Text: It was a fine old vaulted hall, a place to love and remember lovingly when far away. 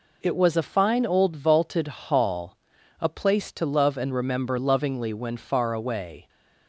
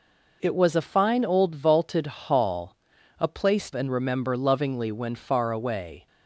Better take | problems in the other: first | skips "to love"; at 3.7 s

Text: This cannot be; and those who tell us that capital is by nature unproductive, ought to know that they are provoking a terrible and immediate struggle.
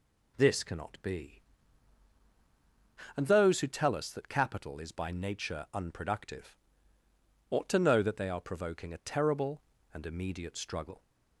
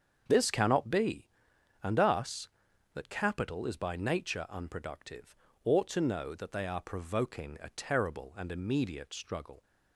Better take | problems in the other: first | starts louder than the rest; strong; until 1.2 s; 7 dB // skips "those who tell"; at 1.9 s

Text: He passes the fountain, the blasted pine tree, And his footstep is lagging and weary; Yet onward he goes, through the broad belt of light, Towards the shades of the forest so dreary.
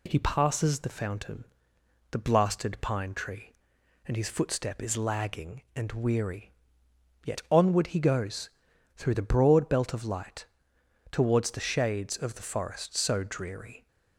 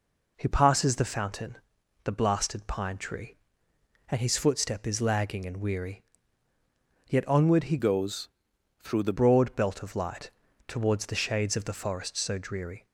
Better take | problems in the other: first | changes voice from "goes" to "the"; from 7.7 to 9.1 s; 1.4 s long

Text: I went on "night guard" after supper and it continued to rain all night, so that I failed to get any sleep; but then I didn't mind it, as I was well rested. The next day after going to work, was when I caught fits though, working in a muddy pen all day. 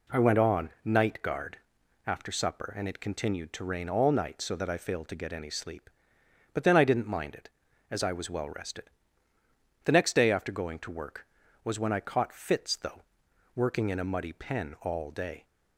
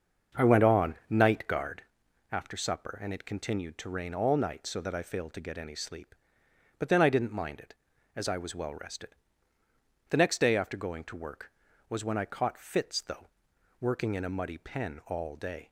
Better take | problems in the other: first | starts louder than the rest; until 1.8 s; 6.5 dB // pauses between "on" and "night"; slight; at 0.9 s; 0.16 s long; slight in the first // pauses between "guard" and "after"; noticeable; at 1.8 s; 0.48 s long; noticeable in the first

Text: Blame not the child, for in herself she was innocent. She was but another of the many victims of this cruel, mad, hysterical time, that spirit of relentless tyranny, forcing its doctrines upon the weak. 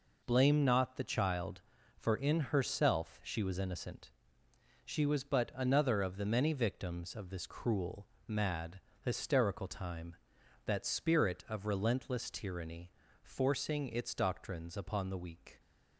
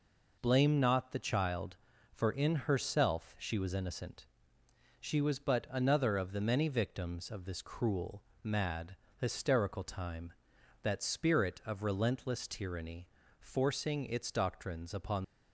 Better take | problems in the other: first | stops before "the weak"; at 15.2 s

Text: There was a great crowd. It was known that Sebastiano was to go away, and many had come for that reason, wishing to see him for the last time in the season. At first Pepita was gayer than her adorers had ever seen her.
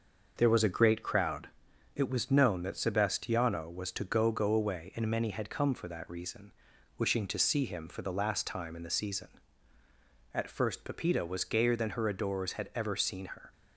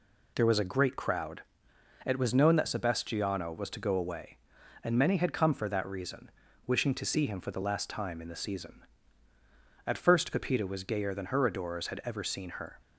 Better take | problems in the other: second | says "go" twice; at 4.2 s

